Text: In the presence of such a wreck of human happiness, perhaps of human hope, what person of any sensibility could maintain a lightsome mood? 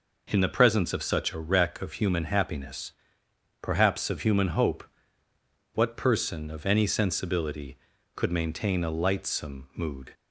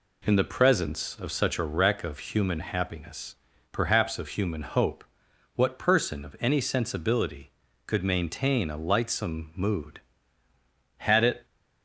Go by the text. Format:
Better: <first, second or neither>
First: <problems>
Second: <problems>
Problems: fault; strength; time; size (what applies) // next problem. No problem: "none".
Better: first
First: none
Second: goes on to say "Had it"; slight; from 10.9 s on; 0.46 s long